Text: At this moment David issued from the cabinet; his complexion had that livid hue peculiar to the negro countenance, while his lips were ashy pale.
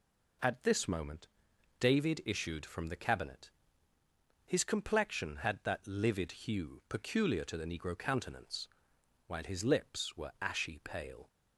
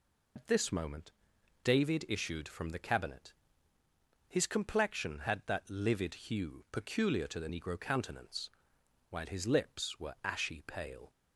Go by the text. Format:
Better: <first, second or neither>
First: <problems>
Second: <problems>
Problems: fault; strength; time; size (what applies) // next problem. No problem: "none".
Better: first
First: pauses between "moment" and "David"; noticeable; at 1.2 s; 0.54 s long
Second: loses the start of "At"; at 0.3 s; 105 ms // pauses between "moment" and "David"; noticeable; at 1.1 s; 0.54 s long